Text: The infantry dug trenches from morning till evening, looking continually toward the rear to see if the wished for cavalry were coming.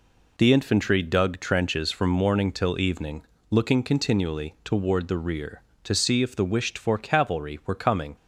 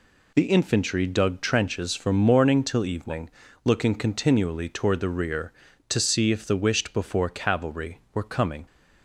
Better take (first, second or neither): first